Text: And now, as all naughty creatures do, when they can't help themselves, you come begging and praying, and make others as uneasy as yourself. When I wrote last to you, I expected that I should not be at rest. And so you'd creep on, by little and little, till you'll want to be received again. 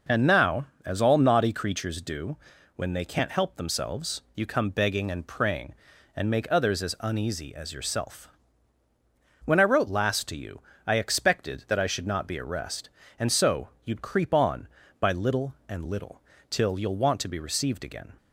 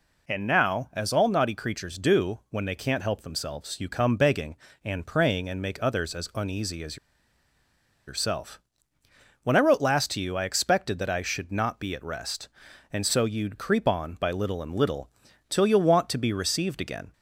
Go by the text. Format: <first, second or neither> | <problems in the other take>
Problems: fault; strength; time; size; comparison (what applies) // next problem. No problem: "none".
first | pauses between "as" and "yourself"; at 6.9 s; 1.1 s long